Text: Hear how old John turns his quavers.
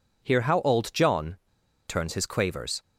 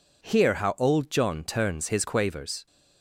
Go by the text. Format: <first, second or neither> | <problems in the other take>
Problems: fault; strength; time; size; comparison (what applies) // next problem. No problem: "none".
second | pauses between "John" and "turns"; noticeable; at 1.3 s; 0.52 s long